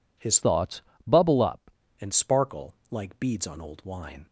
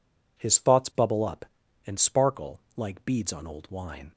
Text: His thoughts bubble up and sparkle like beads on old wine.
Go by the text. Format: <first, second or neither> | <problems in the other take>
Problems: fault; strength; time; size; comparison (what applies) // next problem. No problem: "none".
second | changes voice from "thoughts" to "up"; from 0.4 to 1.6 s; 1.2 s long // pauses between "thoughts" and "bubble"; slight; at 0.8 s; 0.24 s long // pauses between "sparkle" and "like"; slight; at 2.7 s; 0.16 s long; slight in the second